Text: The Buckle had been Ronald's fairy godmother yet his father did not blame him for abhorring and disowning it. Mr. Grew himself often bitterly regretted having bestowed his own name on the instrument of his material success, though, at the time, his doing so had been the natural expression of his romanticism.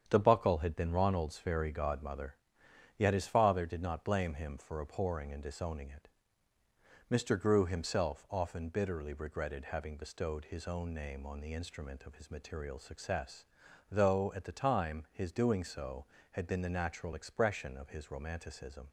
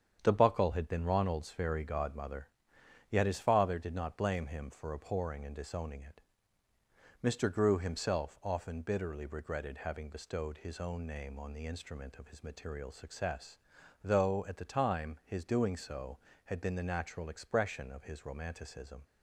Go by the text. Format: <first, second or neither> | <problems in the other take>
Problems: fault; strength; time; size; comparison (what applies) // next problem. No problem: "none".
neither | starts louder than the rest; strong; the same in both // pauses between "godmother" and "yet"; noticeable; the same in both